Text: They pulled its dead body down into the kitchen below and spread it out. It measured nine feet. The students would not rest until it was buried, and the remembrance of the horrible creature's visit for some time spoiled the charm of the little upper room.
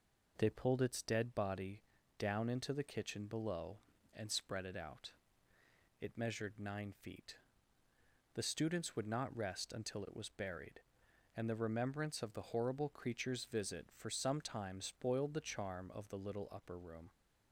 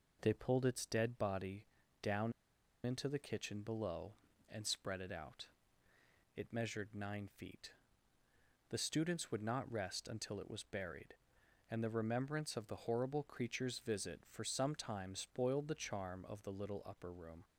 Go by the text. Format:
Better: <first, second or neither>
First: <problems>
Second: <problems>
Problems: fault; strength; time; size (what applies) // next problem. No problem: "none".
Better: first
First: pauses between "body" and "down"; at 1.8 s; 0.38 s long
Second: pauses between "body" and "down"; at 1.6 s; 0.38 s long // pauses between "down" and "into"; noticeable; at 2.3 s; 0.51 s long